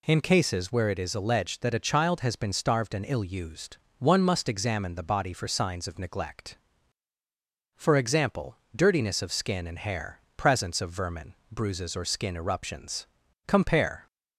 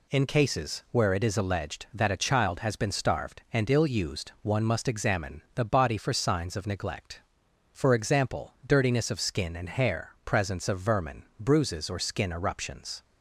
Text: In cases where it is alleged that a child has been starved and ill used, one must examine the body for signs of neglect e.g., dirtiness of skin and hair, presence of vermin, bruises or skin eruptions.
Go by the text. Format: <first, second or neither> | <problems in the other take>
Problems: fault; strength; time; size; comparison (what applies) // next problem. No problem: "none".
second | goes on to say "Compare"; from 13.4 s on; 0.58 s long